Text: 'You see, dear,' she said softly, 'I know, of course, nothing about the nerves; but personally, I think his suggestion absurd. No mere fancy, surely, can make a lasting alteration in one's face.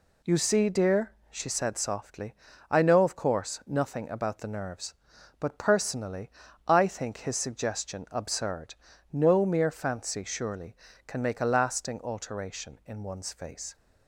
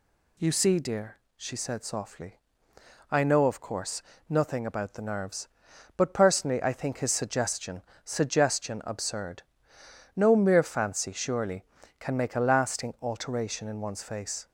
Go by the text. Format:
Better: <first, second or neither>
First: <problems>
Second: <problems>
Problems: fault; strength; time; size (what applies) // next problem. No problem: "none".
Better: first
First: none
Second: says "suggestion" twice; at 8.0 s